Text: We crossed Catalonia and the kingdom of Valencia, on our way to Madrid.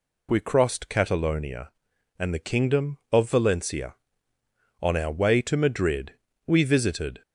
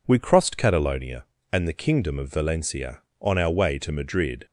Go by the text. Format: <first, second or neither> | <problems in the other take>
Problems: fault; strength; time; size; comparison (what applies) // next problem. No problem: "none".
second | goes on to say "We visited"; noticeable; from 6.4 s on; 0.76 s long